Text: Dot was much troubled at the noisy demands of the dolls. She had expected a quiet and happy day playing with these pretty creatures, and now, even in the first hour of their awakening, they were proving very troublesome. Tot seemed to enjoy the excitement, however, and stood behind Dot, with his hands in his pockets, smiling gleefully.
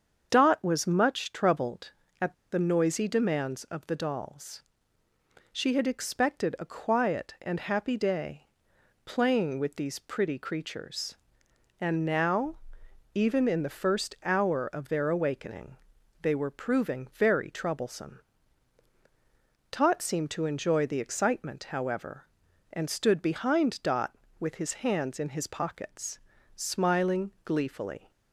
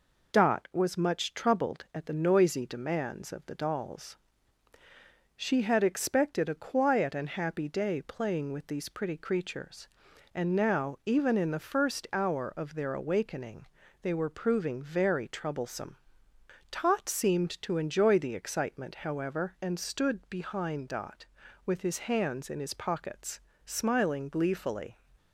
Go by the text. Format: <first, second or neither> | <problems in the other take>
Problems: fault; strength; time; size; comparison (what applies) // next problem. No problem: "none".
second | starts louder than the rest; strong; until 1.3 s; 7 dB // pauses between "at" and "the"; slight; at 2.3 s; 0.17 s long // pauses between "day" and "playing"; noticeable; at 8.4 s; 0.58 s long